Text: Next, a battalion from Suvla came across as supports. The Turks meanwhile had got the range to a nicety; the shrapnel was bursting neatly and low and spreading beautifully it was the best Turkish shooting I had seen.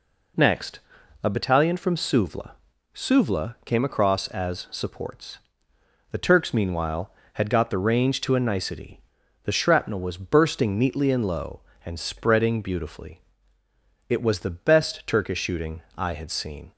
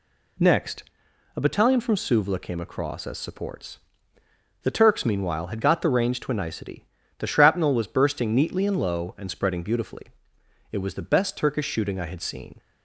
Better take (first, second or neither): second